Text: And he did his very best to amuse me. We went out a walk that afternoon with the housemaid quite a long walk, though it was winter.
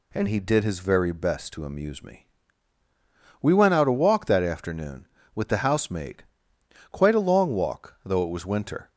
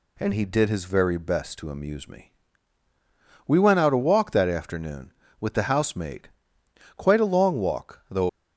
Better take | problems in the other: first | pauses between "housemaid" and "quite"; noticeable; at 6.2 s; 0.66 s long; noticeable in the first // stops before "it was winter"; at 8.2 s

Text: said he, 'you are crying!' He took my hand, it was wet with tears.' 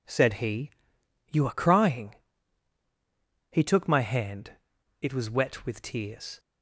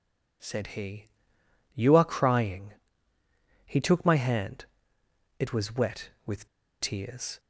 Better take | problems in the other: first | pauses between "with" and "tears"; slight; at 6.4 s; 0.33 s long

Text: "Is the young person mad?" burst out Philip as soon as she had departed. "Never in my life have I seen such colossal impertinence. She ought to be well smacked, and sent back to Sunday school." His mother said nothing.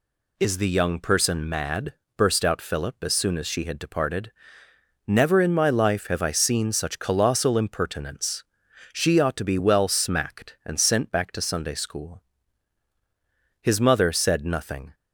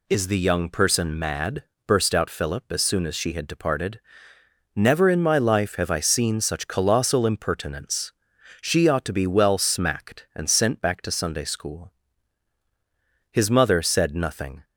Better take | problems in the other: neither | none

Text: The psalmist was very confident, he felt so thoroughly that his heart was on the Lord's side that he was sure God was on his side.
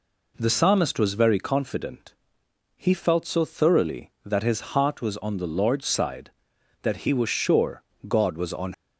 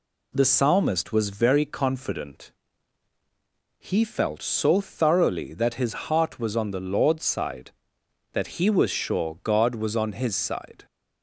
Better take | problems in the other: second | pauses between "sure" and "God"; slight; at 7.8 s; 0.26 s long // stops before "his side"; at 8.7 s

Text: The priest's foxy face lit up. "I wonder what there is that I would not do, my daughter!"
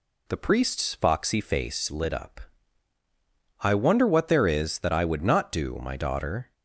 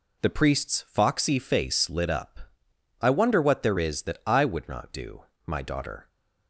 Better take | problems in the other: neither | none

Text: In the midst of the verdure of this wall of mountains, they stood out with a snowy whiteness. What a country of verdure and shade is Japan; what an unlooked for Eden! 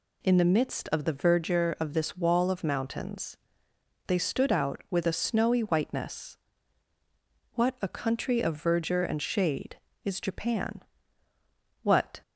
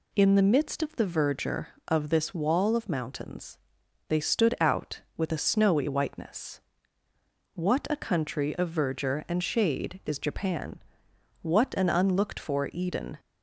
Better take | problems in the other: second | stops before "an unlooked for Eden"; at 12.2 s

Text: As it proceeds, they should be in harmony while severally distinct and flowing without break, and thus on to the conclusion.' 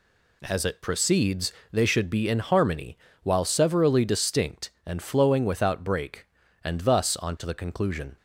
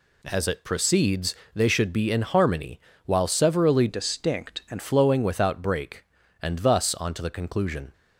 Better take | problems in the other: first | pauses between "harmony" and "while"; slight; at 2.7 s; 0.26 s long; slight in the first // changes voice from "distinct" to "and"; from 3.8 to 4.8 s; 1.0 s long

